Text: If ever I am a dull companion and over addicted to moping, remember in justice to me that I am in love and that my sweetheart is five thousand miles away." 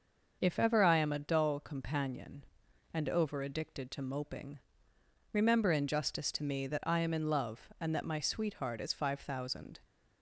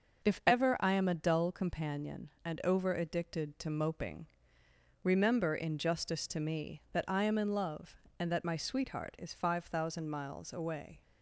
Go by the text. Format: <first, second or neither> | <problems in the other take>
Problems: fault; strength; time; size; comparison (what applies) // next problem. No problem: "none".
second | starts louder than the rest; until 1.4 s; 6 dB; also in the second // stops before "miles away"; at 9.8 s